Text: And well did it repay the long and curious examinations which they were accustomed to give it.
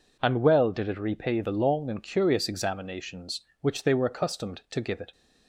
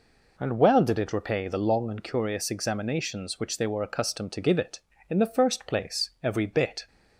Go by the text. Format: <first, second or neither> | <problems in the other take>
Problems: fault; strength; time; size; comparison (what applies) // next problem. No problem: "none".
first | goes on to say "In the first place every bit"; strong; from 5.0 s on; 1.7 s long